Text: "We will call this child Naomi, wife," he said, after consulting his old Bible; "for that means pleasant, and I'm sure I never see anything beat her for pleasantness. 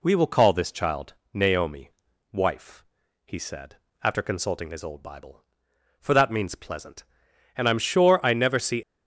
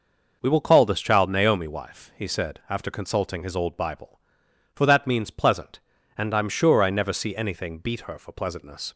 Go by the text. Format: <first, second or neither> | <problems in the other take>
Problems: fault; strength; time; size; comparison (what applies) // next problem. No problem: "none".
second | pauses between "child" and "Naomi"; slight; at 1.1 s; 0.18 s long // stops before "anything beat her for pleasantness"; at 8.8 s